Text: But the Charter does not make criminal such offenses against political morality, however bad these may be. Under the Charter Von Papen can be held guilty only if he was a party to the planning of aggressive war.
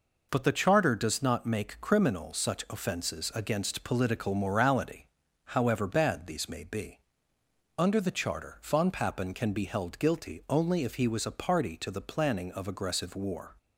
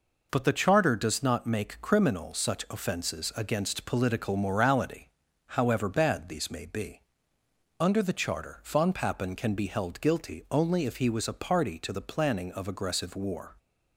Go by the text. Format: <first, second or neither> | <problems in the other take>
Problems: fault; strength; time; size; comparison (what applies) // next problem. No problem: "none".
neither | none